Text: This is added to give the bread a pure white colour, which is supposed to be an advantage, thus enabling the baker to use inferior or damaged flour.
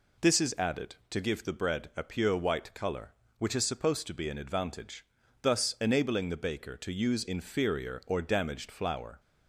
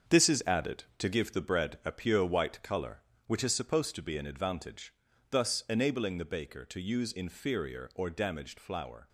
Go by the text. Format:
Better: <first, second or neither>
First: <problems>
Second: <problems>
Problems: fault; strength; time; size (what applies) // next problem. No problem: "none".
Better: first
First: none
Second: gets quieter; strong; throughout; 8 dB